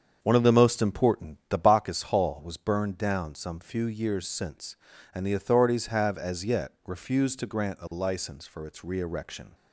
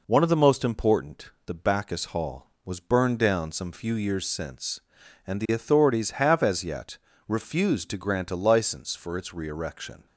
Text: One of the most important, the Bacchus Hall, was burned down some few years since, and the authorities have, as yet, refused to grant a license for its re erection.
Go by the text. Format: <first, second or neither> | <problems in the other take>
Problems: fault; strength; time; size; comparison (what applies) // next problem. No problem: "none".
second | starts louder than the rest; strong; until 1.8 s; 7 dB